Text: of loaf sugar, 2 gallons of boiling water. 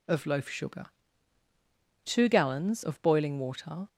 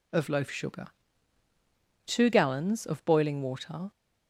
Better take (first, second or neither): neither